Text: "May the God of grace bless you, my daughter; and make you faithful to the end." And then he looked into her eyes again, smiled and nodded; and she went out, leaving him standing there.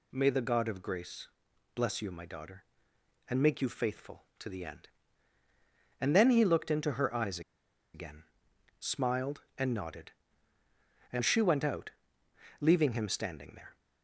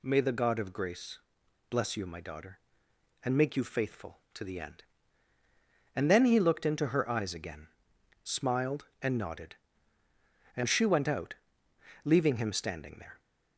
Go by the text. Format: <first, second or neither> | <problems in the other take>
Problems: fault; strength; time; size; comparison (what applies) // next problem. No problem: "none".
second | pauses between "grace" and "bless"; noticeable; at 1.2 s; 0.46 s long; noticeable in the second // pauses between "eyes" and "again"; noticeable; at 7.4 s; 0.53 s long